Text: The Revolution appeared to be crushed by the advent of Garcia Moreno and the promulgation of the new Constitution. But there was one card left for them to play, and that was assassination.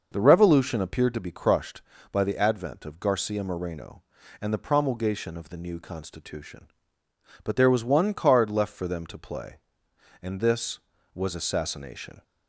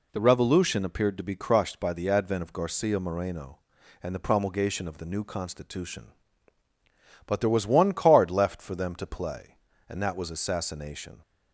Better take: second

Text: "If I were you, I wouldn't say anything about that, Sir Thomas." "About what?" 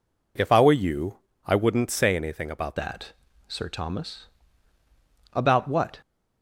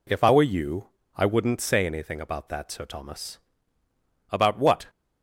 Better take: second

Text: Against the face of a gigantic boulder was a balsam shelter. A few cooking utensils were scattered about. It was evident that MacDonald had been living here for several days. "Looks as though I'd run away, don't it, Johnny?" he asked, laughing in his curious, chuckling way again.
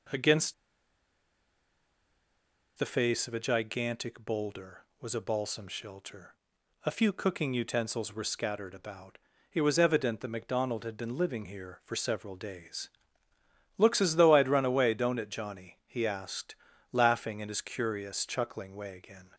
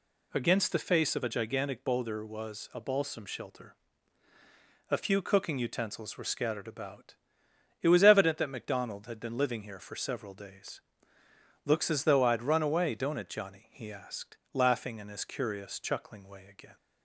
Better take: second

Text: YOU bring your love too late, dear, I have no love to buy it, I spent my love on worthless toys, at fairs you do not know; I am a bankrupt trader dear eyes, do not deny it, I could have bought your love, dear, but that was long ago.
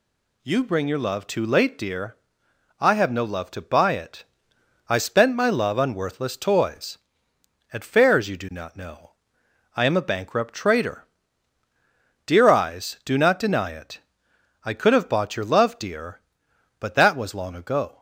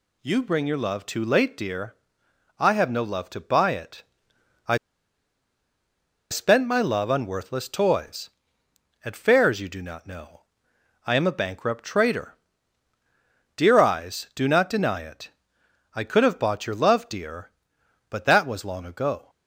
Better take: first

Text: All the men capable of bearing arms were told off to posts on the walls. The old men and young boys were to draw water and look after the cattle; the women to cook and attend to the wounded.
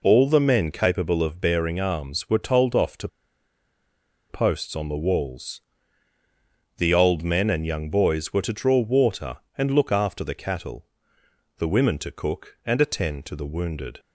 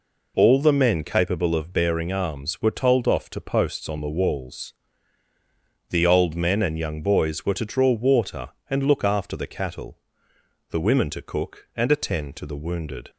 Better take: second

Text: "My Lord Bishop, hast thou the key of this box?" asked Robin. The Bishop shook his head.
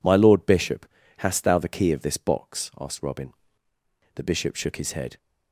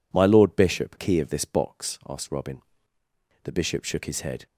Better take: first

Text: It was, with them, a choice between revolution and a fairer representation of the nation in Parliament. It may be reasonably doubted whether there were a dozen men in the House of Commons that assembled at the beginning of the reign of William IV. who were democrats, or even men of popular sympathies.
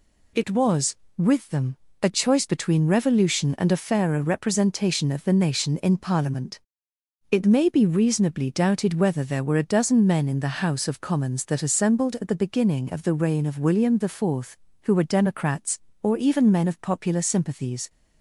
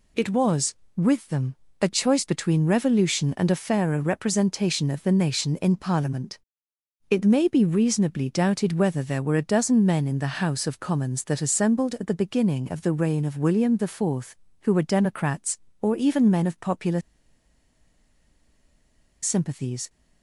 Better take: first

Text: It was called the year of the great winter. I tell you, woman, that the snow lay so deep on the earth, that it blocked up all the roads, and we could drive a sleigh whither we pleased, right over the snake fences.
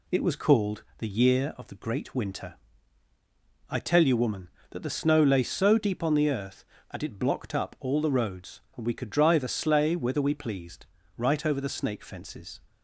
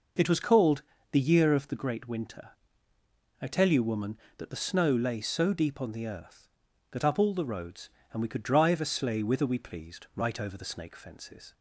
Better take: first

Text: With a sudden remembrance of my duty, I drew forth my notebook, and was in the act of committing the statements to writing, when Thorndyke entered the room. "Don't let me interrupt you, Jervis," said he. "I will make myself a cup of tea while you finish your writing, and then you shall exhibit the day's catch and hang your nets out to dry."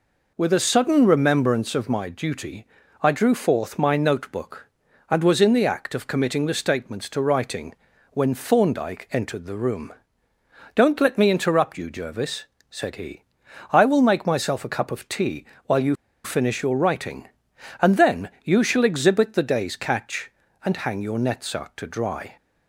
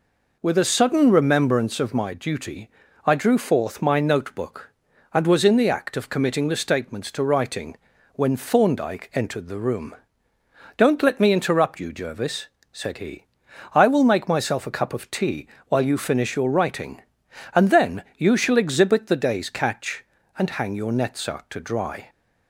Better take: second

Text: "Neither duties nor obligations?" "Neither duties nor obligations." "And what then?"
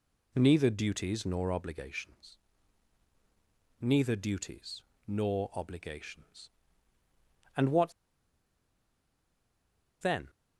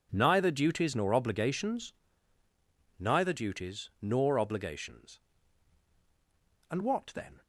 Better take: second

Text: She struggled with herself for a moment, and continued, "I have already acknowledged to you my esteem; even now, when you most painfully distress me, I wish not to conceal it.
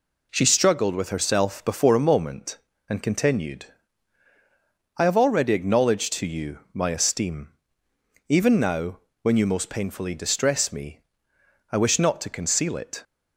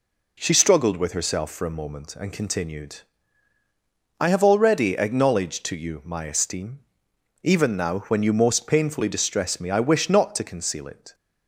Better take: second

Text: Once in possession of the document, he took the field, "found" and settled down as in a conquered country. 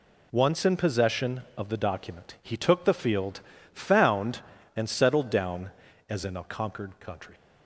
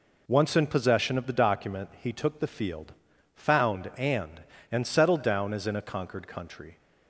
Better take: first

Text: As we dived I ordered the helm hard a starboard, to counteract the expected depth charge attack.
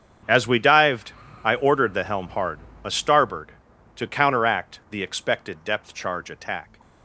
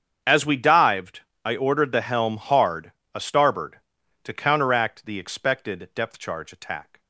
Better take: neither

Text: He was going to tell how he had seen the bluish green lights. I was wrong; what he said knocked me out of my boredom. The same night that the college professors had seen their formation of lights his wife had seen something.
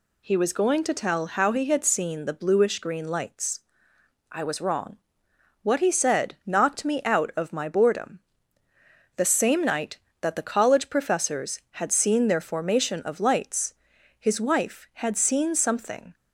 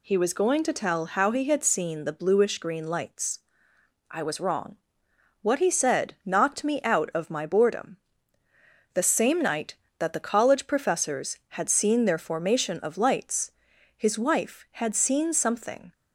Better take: neither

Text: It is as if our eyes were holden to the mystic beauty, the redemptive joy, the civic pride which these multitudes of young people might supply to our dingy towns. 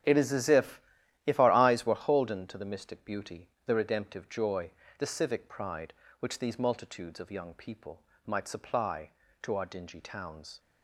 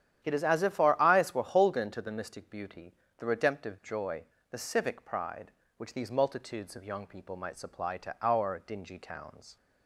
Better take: second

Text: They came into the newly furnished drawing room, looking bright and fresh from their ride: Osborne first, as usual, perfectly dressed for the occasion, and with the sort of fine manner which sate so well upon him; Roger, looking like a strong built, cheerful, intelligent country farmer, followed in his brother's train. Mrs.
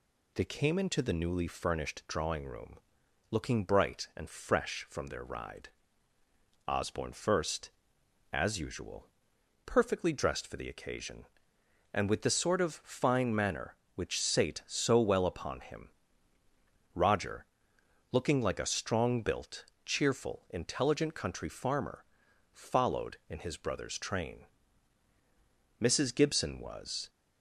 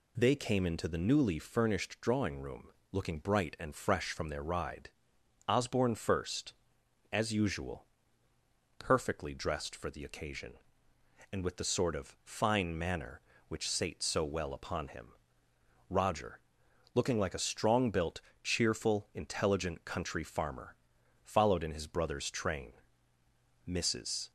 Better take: second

